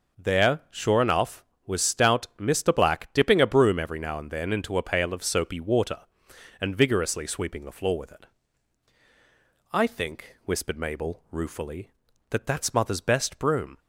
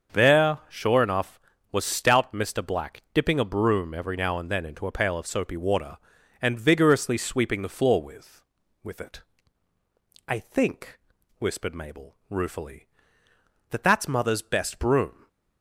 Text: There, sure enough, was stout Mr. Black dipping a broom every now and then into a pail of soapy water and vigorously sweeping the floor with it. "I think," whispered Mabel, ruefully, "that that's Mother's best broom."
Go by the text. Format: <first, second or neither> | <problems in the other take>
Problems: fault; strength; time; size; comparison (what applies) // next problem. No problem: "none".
first | starts louder than the rest; until 1.2 s; 7 dB // says "with" twice; at 8.8 s